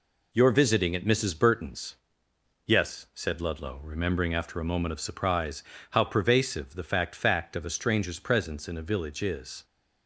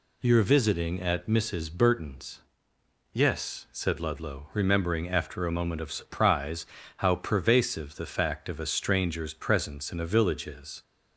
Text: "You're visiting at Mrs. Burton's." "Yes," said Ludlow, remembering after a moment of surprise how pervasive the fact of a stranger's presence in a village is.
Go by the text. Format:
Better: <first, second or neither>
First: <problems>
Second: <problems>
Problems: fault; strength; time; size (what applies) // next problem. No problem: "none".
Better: second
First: pauses between "surprise" and "how"; slight; at 5.6 s; 0.28 s long // says "fact" twice; at 7.1 s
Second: pauses between "surprise" and "how"; slight; at 6.6 s; 0.32 s long